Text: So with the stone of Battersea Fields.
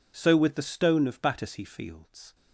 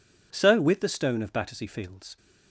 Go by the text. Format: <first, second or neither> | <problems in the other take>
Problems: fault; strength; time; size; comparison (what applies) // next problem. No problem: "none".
neither | none